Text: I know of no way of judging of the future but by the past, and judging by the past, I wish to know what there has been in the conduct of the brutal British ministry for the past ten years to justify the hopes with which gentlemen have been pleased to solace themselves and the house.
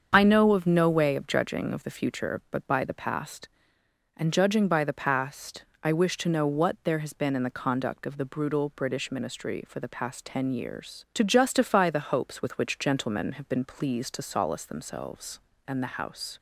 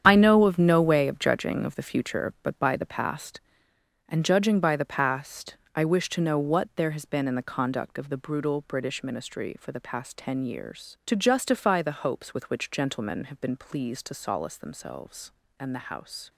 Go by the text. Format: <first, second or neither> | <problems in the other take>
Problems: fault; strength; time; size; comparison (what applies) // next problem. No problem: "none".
first | gets quieter; strong; throughout; 11.5 dB // starts louder than the rest; strong; until 1.0 s; 9 dB; also in the first